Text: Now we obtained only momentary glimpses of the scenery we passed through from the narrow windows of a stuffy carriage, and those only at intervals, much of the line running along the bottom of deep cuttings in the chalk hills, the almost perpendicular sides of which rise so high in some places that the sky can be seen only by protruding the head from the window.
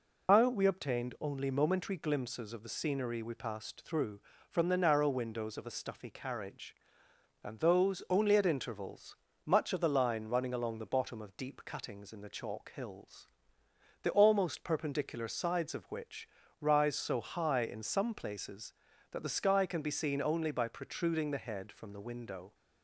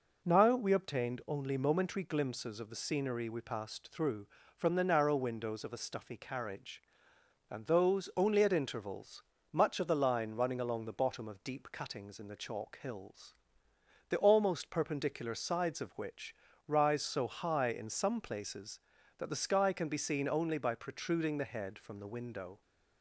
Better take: second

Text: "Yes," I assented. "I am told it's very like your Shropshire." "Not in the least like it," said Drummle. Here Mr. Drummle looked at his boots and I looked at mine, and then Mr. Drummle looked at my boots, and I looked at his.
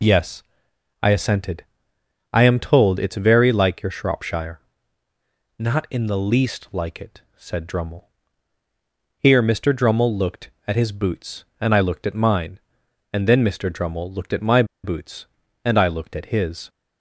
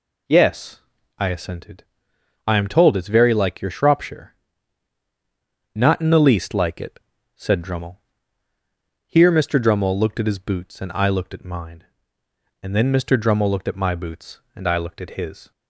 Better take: second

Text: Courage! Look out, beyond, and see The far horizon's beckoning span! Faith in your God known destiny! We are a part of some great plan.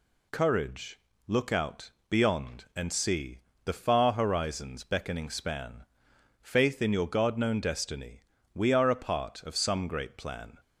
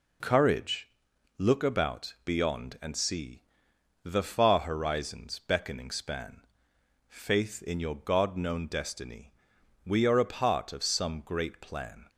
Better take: first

